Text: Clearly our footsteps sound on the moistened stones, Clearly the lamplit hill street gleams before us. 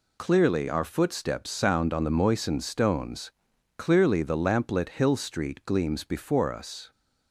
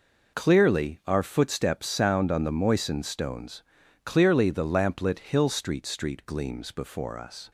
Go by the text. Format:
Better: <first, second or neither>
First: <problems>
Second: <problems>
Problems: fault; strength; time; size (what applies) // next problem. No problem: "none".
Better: first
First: none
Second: says "street" twice; at 5.8 s